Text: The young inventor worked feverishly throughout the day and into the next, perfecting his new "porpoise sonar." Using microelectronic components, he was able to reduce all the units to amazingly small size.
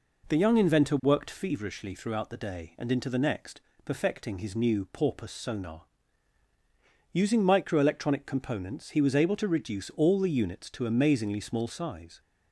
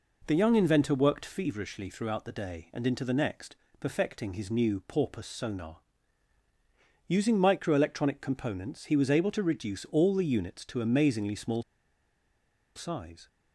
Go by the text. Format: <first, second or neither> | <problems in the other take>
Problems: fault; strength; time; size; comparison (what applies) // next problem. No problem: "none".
first | pauses between "small" and "size"; at 11.6 s; 1.1 s long